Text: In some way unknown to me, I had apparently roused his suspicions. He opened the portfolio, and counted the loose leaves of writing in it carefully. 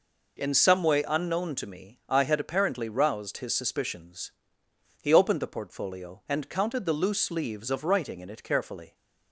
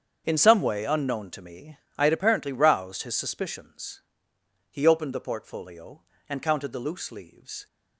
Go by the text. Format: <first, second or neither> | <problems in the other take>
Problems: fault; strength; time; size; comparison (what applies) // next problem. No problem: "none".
first | starts louder than the rest; strong; until 1.2 s; 7.5 dB // stops before "of writing in it carefully"; at 7.6 s